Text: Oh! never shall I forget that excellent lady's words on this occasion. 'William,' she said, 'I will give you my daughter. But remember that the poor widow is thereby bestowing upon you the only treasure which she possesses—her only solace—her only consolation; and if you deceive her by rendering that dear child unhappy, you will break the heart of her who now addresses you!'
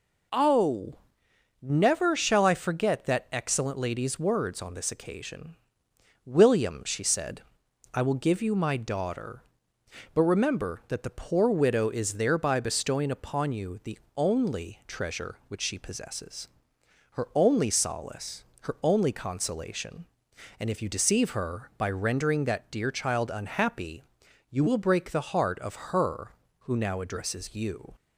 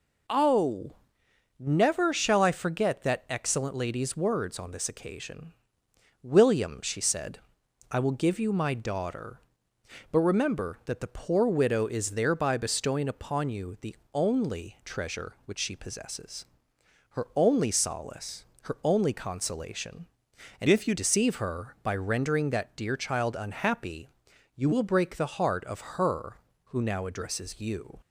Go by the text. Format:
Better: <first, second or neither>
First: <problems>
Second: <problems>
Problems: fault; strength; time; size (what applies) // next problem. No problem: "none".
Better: first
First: pauses between "the" and "only"; slight; at 13.9 s; 0.18 s long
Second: pauses between "the" and "only"; slight; at 13.9 s; 0.18 s long // changes voice from "if" to "you"; from 20.6 to 20.9 s; 0.3 s long